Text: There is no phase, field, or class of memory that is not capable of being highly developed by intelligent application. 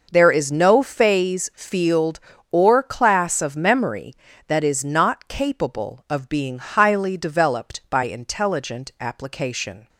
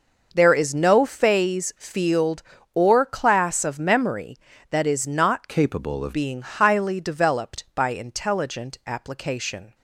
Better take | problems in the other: first | changes voice from "capable" to "of"; from 5.4 to 6.1 s; 0.7 s long

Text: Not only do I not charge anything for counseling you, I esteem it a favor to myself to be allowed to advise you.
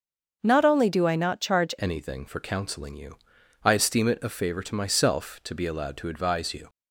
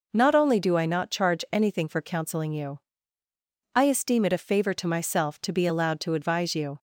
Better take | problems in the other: second | starts louder than the rest; until 1.4 s; 6.5 dB // changes voice at "anything"; from 1.7 s on; 4.9 s long

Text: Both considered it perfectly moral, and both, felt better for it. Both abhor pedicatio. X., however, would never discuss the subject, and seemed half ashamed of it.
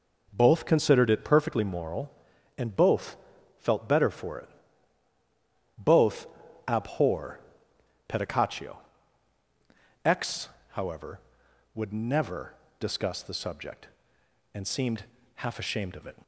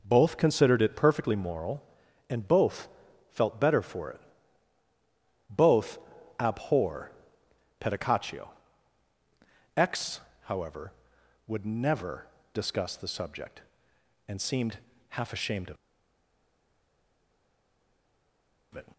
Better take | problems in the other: first | pauses between "Both" and "abhor"; at 5.9 s; 0.40 s long; also in the first // pauses between "abhor" and "pedicatio"; noticeable; at 7.1 s; 0.68 s long; noticeable in the first // pauses between "never" and "discuss"; slight; at 12.2 s; 0.26 s long; slight in the first // pauses between "seemed" and "half"; slight; at 14.7 s; 0.32 s long; slight in the first // pauses between "of" and "it"; strong; at 15.7 s; 2.9 s long

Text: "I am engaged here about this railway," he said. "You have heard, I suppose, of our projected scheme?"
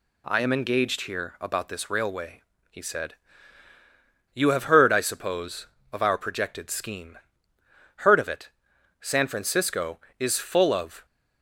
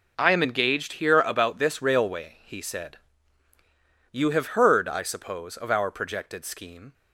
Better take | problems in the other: second | goes on to say "Heard of it San Francisco is full of"; strong; from 7.9 s on; 3.0 s long

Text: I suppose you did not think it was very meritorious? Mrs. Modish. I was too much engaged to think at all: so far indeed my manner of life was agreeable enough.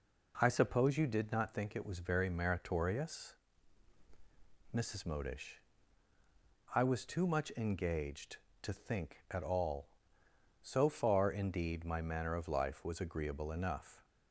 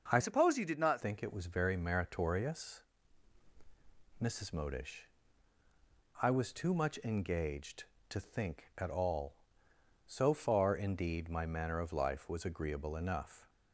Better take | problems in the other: first | starts louder than the rest; until 1.1 s; 6 dB // changes voice from "suppose" to "not"; from 0.2 to 1.0 s; 0.8 s long

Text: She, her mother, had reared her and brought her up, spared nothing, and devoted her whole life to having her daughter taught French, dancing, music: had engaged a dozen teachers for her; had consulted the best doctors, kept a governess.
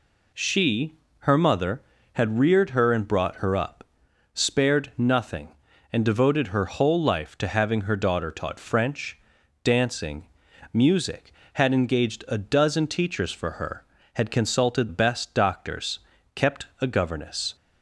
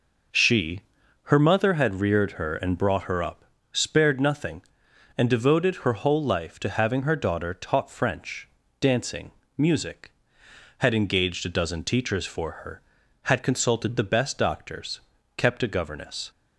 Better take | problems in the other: second | skips "the"; at 14.8 s

